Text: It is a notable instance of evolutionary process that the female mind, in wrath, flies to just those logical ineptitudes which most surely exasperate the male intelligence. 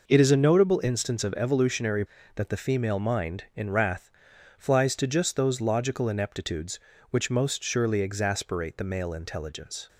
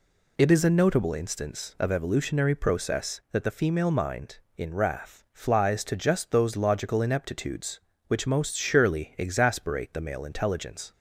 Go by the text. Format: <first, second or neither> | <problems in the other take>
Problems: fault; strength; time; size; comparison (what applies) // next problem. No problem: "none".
second | skips "process"; at 2.1 s